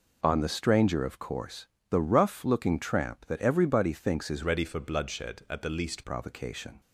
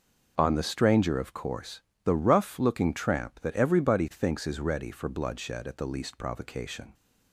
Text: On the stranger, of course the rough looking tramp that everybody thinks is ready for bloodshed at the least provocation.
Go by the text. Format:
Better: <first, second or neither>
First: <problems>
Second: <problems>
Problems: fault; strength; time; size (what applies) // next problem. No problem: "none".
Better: second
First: pauses between "course" and "the"; slight; at 1.6 s; 0.24 s long // changes voice from "ready" to "least"; from 4.4 to 6.0 s; 1.6 s long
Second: pauses between "course" and "the"; slight; at 1.7 s; 0.24 s long